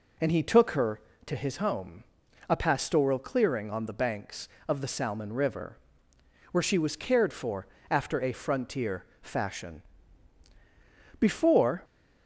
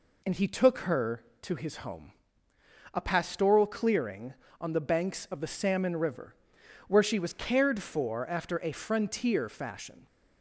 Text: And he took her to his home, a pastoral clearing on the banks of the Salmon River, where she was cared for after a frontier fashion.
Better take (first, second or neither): second